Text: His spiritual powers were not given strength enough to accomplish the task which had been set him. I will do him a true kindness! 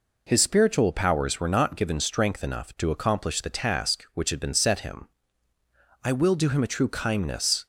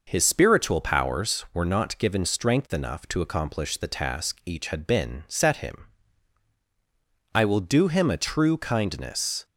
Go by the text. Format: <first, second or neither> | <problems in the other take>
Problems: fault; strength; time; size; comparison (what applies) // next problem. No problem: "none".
first | says "each" for "which"; at 4.4 s